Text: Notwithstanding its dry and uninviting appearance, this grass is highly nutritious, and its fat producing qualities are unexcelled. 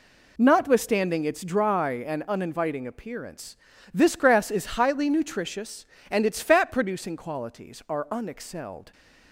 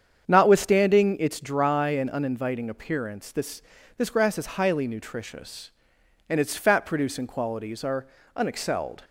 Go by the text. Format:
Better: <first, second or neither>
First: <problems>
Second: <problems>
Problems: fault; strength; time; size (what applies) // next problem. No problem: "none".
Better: first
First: none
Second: starts louder than the rest; strong; until 1.2 s; 7.5 dB // says "this" twice; at 3.9 s // pauses between "are" and "unexcelled"; slight; at 8.0 s; 0.28 s long